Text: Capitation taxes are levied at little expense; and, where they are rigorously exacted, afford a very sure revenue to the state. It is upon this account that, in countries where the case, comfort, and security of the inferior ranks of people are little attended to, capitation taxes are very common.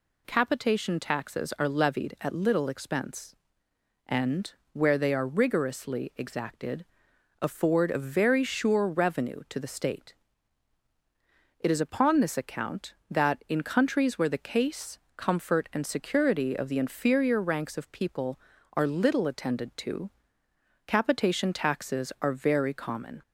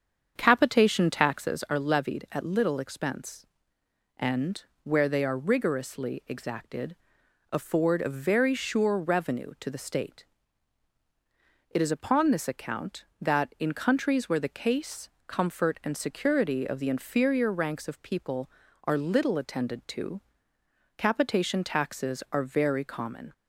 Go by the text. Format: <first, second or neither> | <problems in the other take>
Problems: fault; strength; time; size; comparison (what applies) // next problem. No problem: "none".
first | starts louder than the rest; strong; until 1.6 s; 7.5 dB